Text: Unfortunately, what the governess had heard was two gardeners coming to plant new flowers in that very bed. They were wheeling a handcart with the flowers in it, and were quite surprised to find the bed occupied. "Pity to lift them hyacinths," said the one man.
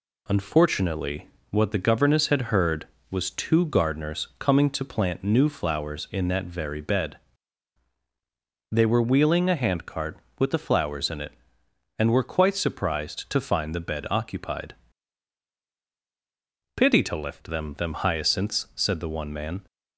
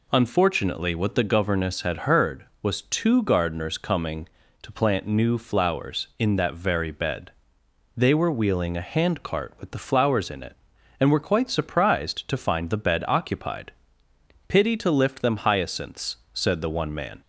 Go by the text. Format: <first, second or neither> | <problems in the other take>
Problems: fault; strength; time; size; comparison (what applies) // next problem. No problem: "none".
second | says "them" twice; at 17.7 s